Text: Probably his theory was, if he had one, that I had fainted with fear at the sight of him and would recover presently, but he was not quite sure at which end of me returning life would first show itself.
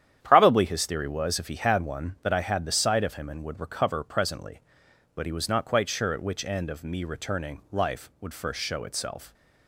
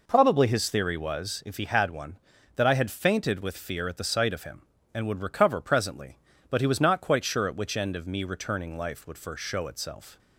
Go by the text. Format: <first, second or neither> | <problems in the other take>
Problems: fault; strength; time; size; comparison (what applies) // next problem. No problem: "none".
second | starts louder than the rest; strong; until 1.2 s; 10 dB // skips "fainted with fear at"; at 2.6 s